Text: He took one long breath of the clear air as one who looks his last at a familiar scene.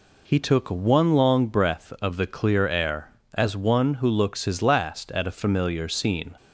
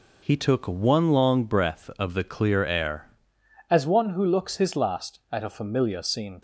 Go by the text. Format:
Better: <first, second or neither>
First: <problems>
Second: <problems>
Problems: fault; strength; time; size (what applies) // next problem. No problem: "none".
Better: first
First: none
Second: changes voice at "as"; from 3.7 s on; 2.7 s long